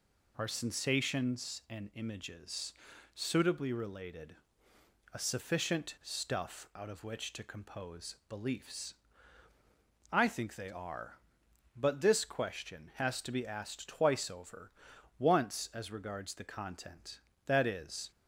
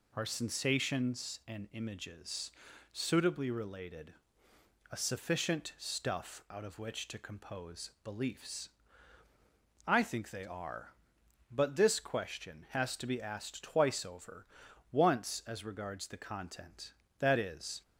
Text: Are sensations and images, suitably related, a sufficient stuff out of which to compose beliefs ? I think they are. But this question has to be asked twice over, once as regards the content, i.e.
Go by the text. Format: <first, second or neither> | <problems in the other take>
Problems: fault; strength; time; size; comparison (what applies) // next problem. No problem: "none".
neither | none